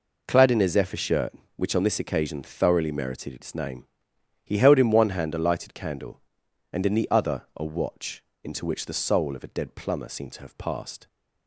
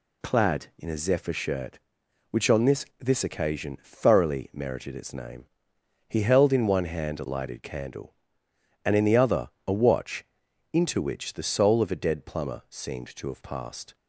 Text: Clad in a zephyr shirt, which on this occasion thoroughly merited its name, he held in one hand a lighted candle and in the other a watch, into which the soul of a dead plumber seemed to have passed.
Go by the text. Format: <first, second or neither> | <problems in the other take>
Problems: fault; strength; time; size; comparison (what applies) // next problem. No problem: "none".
first | says "this" twice; at 2.9 s // pauses between "other" and "a"; slight; at 9.4 s; 0.16 s long